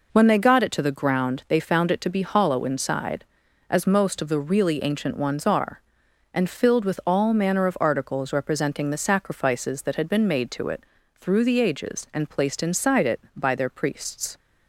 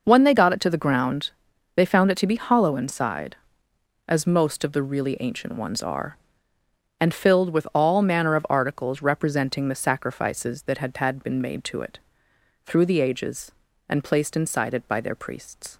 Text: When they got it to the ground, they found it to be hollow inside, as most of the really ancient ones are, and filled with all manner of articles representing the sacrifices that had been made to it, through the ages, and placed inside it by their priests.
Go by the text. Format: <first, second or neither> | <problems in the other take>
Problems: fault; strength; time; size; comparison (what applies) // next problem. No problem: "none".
first | says "had" twice; at 10.9 s